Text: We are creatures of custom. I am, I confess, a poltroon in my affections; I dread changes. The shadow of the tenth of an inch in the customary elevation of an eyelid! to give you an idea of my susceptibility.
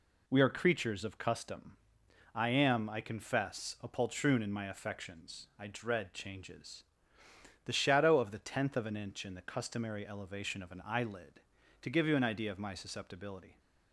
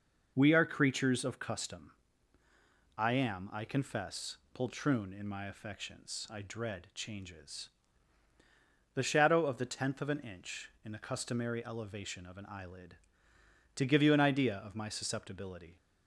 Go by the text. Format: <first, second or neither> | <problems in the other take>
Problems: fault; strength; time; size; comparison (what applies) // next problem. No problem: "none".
first | skips "a"; at 4.4 s